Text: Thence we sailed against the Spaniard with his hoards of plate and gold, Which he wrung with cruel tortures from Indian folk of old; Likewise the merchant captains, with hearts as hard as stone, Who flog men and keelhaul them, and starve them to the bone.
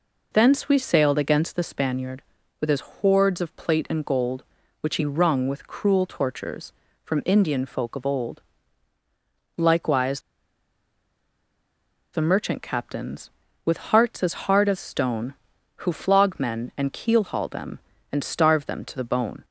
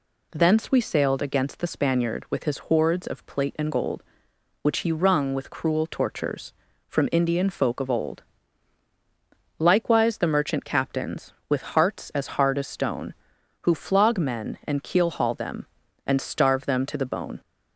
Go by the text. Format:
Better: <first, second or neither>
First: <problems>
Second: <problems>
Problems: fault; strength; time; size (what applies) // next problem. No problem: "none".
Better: second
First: pauses between "Likewise" and "the"; strong; at 10.2 s; 1.9 s long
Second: none